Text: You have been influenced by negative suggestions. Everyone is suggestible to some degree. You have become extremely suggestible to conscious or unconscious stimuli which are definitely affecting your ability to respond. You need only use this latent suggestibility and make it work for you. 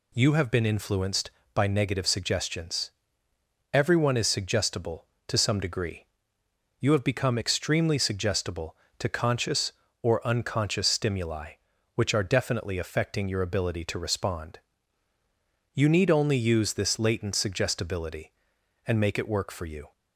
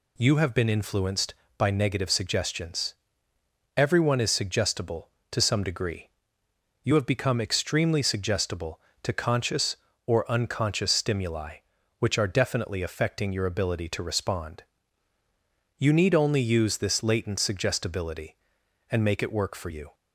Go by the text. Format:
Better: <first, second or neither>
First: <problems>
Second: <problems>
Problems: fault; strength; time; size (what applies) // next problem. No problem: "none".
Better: neither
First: none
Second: none